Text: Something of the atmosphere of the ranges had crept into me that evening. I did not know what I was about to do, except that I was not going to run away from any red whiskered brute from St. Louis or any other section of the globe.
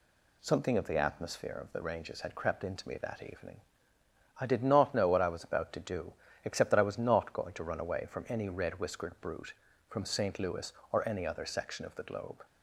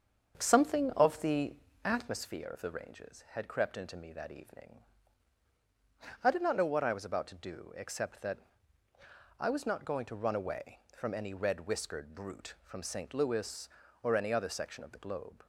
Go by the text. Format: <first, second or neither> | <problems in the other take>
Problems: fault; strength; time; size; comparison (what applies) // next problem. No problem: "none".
first | starts louder than the rest; strong; until 2.2 s; 7.5 dB // pauses between "the" and "atmosphere"; slight; at 1.5 s; 0.30 s long // pauses between "that" and "I"; at 8.3 s; 1.0 s long